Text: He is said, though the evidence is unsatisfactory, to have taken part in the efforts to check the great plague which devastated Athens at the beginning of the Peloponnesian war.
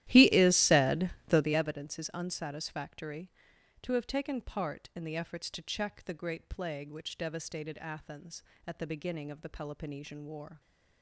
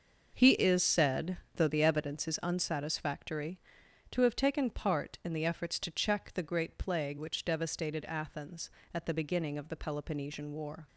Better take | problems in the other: second | starts louder than the rest; strong; until 1.6 s; 13.5 dB

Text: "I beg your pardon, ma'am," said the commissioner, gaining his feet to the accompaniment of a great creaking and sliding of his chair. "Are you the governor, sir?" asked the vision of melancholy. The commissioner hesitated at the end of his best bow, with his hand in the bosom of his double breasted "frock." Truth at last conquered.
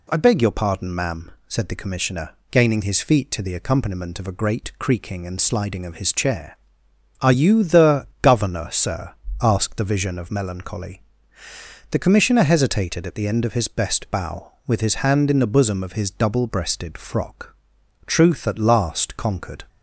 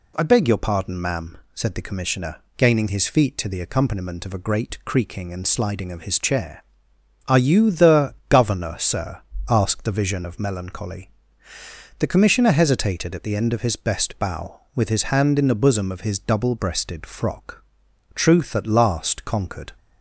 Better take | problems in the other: neither | none

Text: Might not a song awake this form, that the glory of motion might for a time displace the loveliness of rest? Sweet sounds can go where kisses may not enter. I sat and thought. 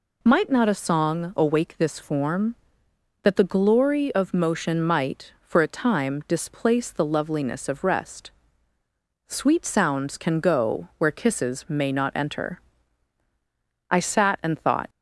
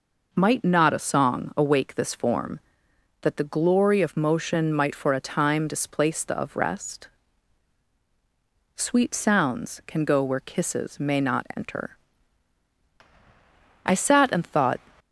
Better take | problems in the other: first | skips "loveliness"; at 6.3 s

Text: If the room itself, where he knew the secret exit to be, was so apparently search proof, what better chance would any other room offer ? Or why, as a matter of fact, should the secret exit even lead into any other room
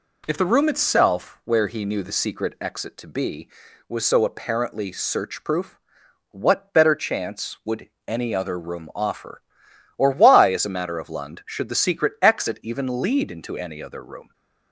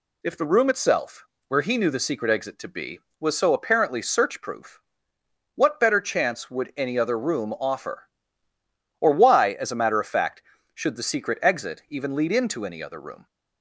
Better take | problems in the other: second | pauses between "would" and "any"; slight; at 7.8 s; 0.18 s long // says "lund" for "fact"; at 11.1 s

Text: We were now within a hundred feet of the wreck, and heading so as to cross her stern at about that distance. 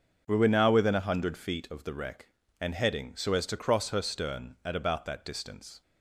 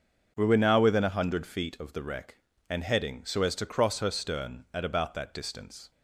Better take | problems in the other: neither | starts louder than the rest; the same in both

